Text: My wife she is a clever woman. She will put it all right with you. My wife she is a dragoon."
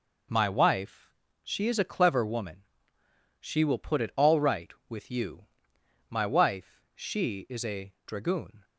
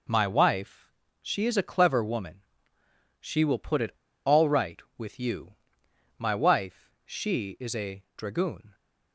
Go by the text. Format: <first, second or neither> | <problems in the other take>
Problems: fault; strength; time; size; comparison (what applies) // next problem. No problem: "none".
first | pauses between "wife" and "she"; slight; at 0.8 s; 0.32 s long; slight in the first // pauses between "it" and "all"; slight; at 3.9 s; 0.34 s long // pauses between "wife" and "she"; slight; at 6.9 s; 0.16 s long // pauses between "a" and "dragoon"; slight; at 8.0 s; 0.16 s long; slight in the first